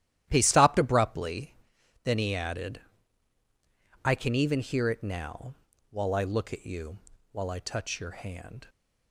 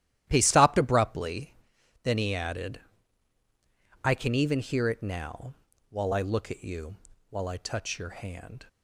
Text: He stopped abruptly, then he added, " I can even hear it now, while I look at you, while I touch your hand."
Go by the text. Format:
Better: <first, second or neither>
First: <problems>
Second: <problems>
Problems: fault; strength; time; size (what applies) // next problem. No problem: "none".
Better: neither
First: starts louder than the rest; strong; until 1.3 s; 12 dB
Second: starts louder than the rest; strong; until 1.3 s; 12 dB